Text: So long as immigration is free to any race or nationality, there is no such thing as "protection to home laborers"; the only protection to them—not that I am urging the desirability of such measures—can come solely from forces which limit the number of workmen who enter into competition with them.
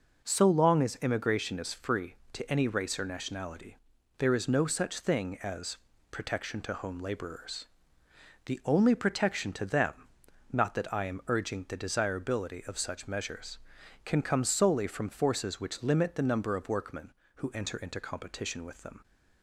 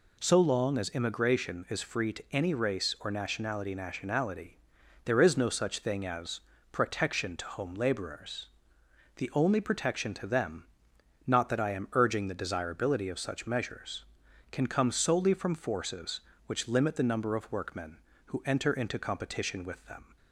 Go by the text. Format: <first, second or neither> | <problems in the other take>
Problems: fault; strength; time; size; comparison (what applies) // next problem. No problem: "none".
first | says "nationality" twice; at 3.7 s // pauses between "as" and "protection"; slight; at 6.3 s; 0.32 s long; slight in the first